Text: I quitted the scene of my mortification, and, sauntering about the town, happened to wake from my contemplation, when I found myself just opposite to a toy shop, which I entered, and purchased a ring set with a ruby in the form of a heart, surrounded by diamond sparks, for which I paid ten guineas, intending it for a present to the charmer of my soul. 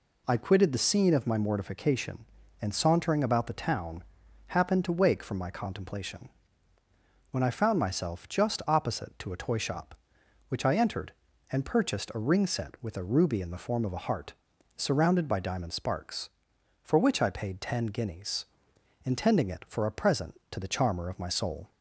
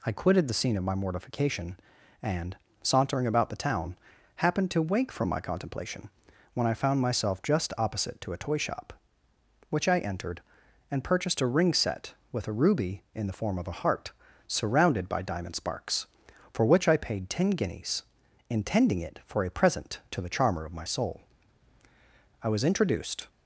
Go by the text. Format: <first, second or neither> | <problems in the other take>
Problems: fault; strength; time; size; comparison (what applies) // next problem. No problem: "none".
first | goes on to say "I was introduced"; noticeable; from 22.4 s on; 0.86 s long